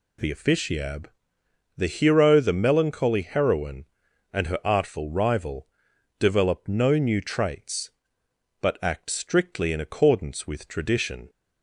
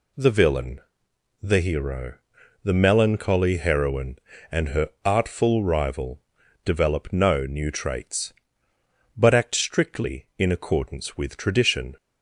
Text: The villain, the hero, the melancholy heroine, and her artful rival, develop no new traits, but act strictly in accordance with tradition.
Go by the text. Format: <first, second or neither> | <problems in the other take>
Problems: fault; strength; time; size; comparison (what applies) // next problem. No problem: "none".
second | says "officiab" for "villain"; at 0.3 s